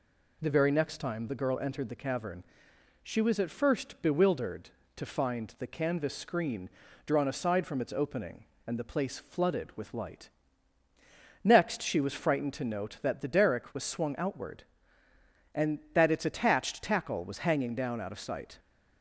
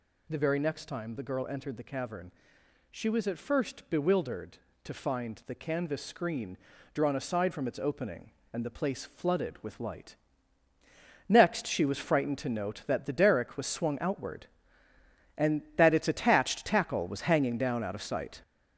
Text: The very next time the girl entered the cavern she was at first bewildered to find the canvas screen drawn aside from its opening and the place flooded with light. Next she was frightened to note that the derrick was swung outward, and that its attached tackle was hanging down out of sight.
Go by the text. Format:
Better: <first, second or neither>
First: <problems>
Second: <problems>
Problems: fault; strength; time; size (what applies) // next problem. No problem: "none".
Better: first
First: pauses between "cavern" and "she"; noticeable; at 2.4 s; 0.58 s long // pauses between "screen" and "drawn"; slight; at 6.6 s; 0.36 s long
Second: gets louder; throughout; 7 dB // pauses between "cavern" and "she"; noticeable; at 2.3 s; 0.58 s long // pauses between "screen" and "drawn"; slight; at 6.5 s; 0.36 s long